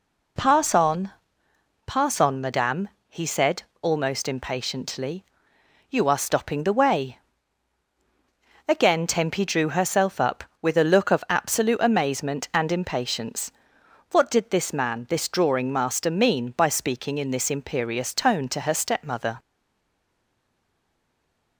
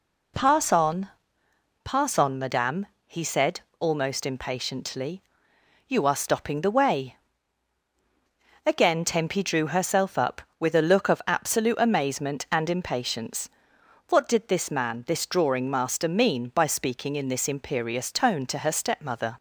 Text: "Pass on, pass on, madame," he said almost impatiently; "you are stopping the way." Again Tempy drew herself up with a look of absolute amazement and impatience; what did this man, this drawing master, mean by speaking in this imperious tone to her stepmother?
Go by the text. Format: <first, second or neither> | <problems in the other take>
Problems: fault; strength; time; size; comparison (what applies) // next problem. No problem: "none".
second | pauses between "said" and "almost"; slight; at 3.6 s; 0.18 s long; slight in the second // stays silent after the last word; from 19.3 s on; 2.2 s long